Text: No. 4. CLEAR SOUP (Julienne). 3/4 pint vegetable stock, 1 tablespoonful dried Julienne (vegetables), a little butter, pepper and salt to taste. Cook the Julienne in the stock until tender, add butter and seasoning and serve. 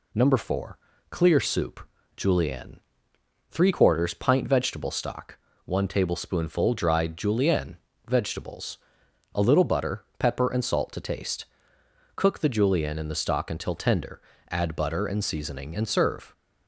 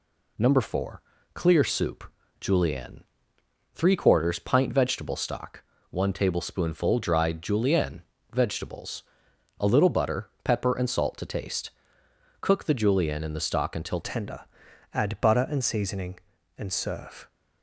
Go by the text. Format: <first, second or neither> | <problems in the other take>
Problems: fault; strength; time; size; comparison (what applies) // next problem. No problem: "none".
first | changes voice at "tender"; from 14.0 s on; 3.2 s long